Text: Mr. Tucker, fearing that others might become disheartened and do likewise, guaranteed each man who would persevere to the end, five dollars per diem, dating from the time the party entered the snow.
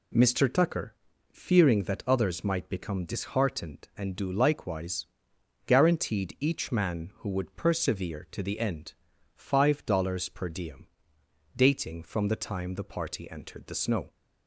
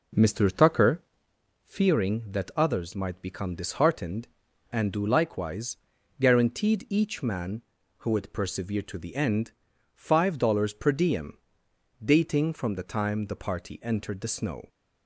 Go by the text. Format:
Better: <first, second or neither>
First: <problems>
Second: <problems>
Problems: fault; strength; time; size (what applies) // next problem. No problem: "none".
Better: first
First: none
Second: starts louder than the rest; noticeable; until 1.4 s; 4.5 dB